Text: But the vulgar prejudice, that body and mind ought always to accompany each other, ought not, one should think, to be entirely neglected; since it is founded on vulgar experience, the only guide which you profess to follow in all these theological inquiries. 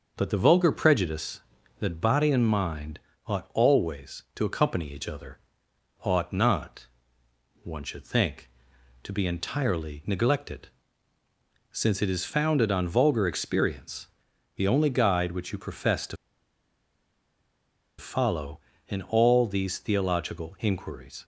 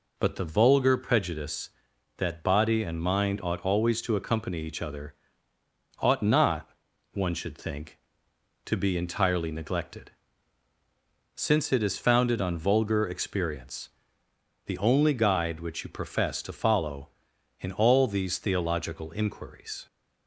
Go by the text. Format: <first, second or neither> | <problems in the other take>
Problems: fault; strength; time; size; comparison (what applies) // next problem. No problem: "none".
second | starts louder than the rest; noticeable; until 1.1 s; 6 dB // pauses between "mind" and "ought"; slight; at 3.0 s; 0.26 s long // pauses between "to" and "follow"; strong; at 16.1 s; 1.8 s long